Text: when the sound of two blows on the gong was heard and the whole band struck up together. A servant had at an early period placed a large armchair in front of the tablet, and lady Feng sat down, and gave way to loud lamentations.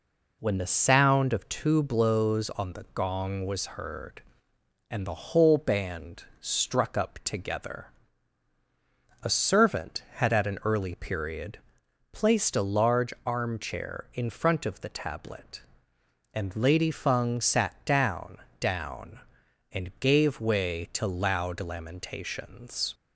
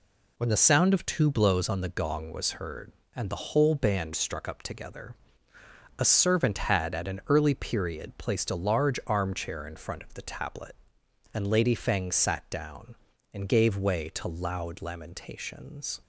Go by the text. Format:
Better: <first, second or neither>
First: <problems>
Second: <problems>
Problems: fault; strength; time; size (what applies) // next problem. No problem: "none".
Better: second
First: pauses between "band" and "struck"; slight; at 6.2 s; 0.16 s long // pauses between "period" and "placed"; noticeable; at 11.5 s; 0.54 s long // says "down" twice; at 18.5 s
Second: none